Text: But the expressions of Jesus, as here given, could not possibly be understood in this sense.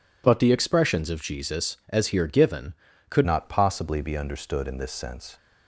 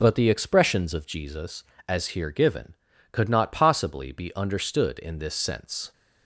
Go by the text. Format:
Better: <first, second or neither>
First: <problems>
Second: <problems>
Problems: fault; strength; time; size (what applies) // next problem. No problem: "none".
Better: second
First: changes voice at "not"; from 3.2 s on; 2.1 s long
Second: none